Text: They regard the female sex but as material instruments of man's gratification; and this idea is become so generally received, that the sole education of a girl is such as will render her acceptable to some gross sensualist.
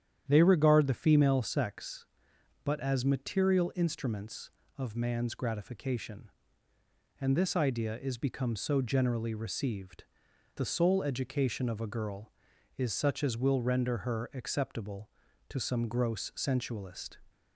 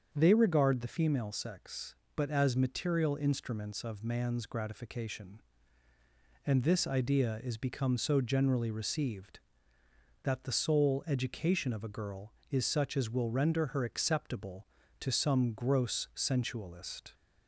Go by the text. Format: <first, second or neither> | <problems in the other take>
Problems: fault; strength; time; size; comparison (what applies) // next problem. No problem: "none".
second | starts louder than the rest; strong; until 1.2 s; 10 dB; strong in the second // skips "that"; at 10.3 s